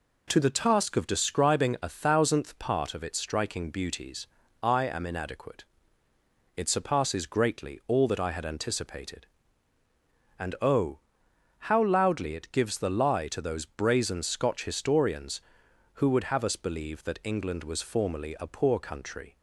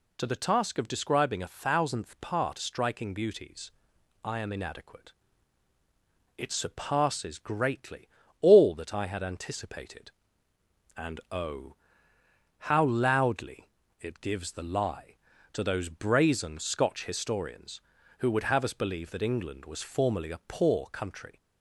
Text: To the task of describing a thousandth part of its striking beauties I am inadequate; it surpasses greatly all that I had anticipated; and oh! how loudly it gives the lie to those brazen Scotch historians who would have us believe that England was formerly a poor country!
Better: first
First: pauses between "beauties" and "I"; slight; at 4.2 s; 0.36 s long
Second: skips "of its"; at 2.6 s // pauses between "beauties" and "I"; noticeable; at 3.7 s; 0.52 s long // pauses between "greatly" and "all"; slight; at 8.0 s; 0.36 s long // pauses between "loudly" and "it"; slight; at 13.7 s; 0.28 s long

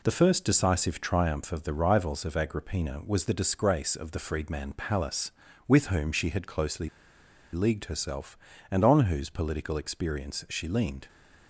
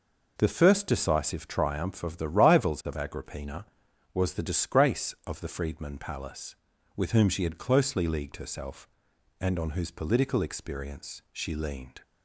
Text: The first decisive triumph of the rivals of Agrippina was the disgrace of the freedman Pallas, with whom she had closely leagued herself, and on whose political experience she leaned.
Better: second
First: pauses between "closely" and "leagued"; noticeable; at 6.8 s; 0.66 s long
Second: none

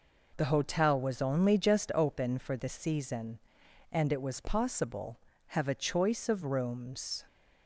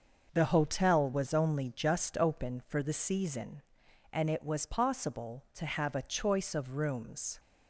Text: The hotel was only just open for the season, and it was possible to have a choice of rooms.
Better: second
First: skips "to"; at 5.3 s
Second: none

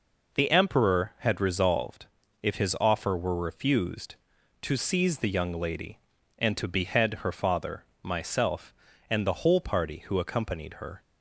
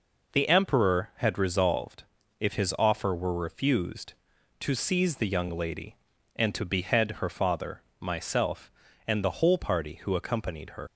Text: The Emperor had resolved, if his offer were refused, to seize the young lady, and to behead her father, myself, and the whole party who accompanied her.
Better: first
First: none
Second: leaves "her" unfinished; at 10.8 s; 105 ms

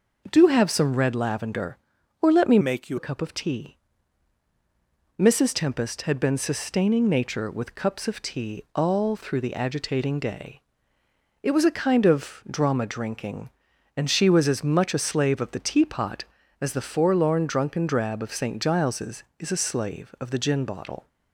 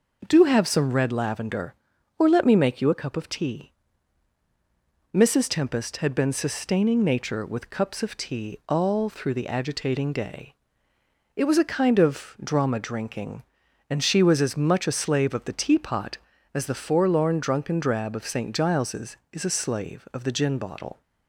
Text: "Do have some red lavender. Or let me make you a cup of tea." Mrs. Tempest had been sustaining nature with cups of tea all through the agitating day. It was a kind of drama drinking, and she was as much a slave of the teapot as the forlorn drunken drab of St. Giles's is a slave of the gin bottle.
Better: second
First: changes voice from "make" to "you"; from 2.6 to 2.9 s; 0.3 s long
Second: none

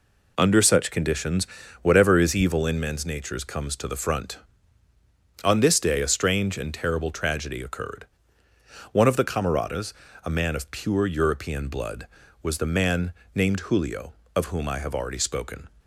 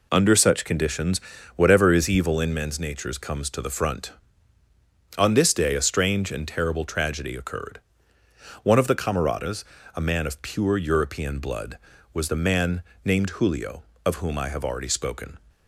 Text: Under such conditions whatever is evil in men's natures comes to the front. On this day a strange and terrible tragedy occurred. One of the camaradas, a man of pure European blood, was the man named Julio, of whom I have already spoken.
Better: neither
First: pauses between "conditions" and "whatever"; slight; at 1.4 s; 0.36 s long // pauses between "man" and "named"; slight; at 13.1 s; 0.20 s long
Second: pauses between "conditions" and "whatever"; slight; at 1.2 s; 0.36 s long // pauses between "man" and "named"; slight; at 12.8 s; 0.20 s long

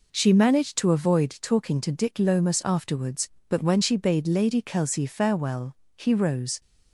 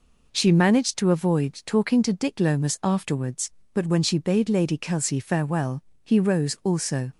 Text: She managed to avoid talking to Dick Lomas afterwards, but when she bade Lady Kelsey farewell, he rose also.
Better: second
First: stops before "also"; at 6.6 s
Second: none

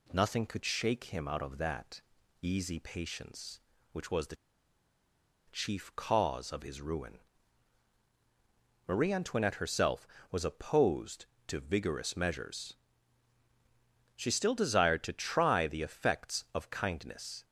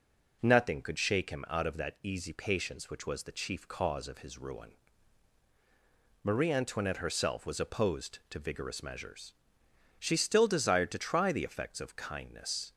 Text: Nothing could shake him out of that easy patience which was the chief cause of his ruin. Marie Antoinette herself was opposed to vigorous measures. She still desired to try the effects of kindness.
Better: second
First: pauses between "that" and "easy"; at 2.0 s; 0.38 s long // pauses between "the" and "chief"; at 4.3 s; 1.1 s long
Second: none

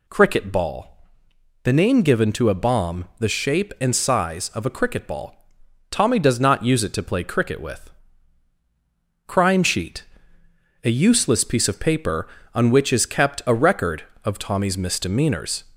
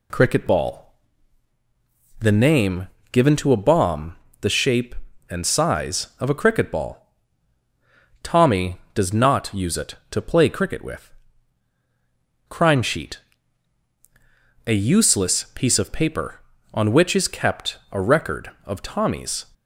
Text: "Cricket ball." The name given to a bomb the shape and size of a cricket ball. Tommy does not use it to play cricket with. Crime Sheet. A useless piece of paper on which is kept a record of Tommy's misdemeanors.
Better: first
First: none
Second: pauses between "name" and "given"; slight; at 2.8 s; 0.24 s long // pauses between "bomb" and "the"; slight; at 4.1 s; 0.24 s long // stops before "misdemeanors"; at 19.5 s

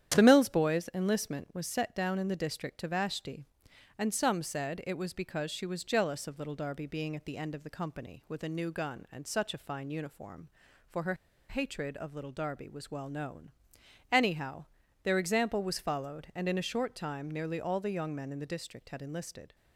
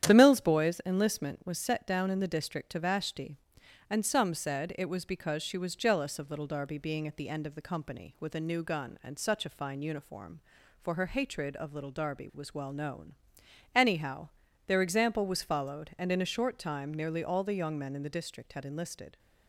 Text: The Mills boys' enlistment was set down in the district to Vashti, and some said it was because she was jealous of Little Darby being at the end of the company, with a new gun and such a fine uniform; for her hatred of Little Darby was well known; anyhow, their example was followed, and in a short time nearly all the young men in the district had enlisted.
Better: second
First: starts louder than the rest; strong; until 1.1 s; 10 dB // pauses between "her" and "hatred"; slight; at 11.1 s; 0.34 s long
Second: starts louder than the rest; strong; until 1.0 s; 10 dB

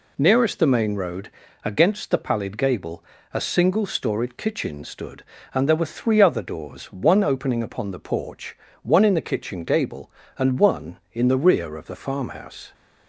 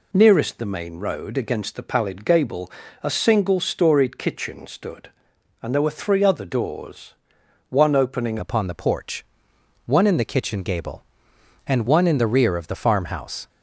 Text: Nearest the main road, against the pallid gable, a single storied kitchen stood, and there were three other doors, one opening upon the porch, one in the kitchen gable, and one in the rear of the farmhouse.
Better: first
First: none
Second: changes voice at "upon"; from 8.3 s on; 5.1 s long

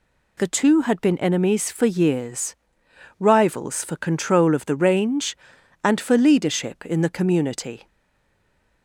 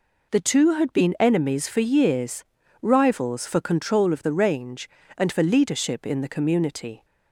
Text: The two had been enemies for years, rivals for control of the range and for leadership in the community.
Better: second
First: stays silent after the last word; from 7.8 s on; 1.0 s long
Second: none

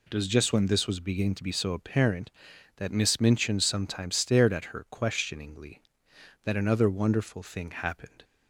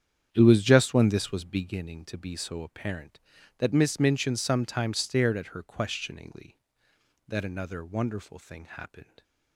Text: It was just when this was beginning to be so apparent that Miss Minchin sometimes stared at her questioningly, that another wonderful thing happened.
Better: first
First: none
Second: starts louder than the rest; strong; until 1.7 s; 8.5 dB

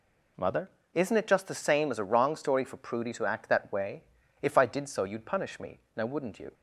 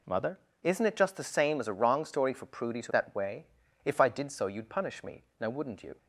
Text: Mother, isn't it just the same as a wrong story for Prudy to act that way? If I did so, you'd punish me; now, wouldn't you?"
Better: first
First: none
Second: skips "act"; at 2.9 s

